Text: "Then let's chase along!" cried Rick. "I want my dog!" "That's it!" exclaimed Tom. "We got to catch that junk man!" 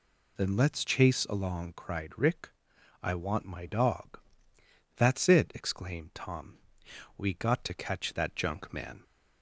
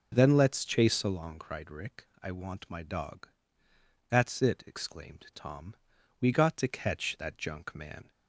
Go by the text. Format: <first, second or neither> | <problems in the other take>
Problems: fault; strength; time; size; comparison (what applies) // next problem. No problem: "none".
neither | none